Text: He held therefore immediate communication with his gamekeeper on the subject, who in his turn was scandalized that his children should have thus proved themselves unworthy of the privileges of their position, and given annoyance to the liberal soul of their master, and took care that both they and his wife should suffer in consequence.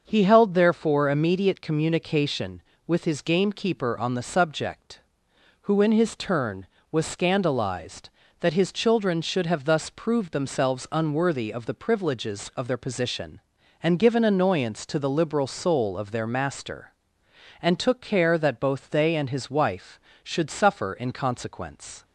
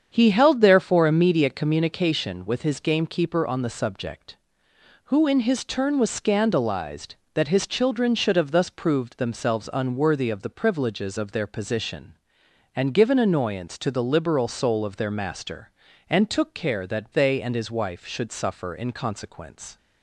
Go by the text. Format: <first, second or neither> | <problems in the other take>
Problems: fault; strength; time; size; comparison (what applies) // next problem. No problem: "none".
first | starts louder than the rest; strong; until 1.1 s; 7.5 dB; also in the first // skips "both"; at 17.1 s